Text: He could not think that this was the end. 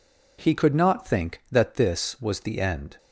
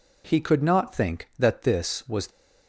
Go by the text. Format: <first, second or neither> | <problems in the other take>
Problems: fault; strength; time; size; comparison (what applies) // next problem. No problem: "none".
first | stops before "the end"; at 2.2 s